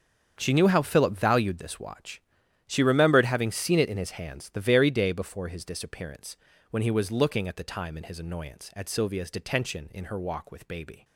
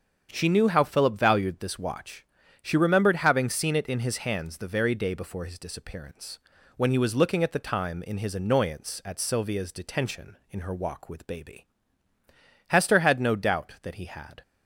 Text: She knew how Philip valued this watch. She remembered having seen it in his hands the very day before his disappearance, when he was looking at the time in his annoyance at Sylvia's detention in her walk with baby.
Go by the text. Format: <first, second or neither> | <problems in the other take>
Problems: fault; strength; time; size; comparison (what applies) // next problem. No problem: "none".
first | starts louder than the rest; strong; until 1.3 s; 7.5 dB; strong in the first // goes on to say "Hester had no doubt that he had"; strong; from 12.6 s on; 1.7 s long